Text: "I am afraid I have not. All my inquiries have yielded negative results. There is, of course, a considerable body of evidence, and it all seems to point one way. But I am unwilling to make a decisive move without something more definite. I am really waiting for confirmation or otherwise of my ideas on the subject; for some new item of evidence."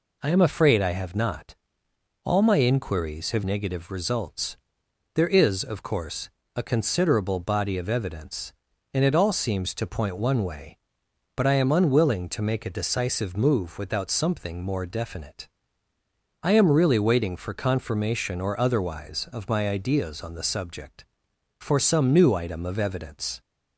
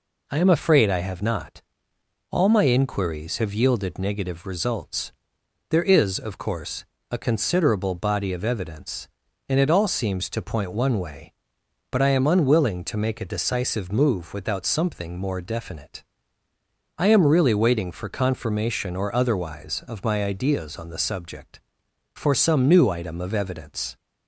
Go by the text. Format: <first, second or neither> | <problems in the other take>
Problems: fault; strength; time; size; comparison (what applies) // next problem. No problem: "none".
second | skips "yielded"; at 3.4 s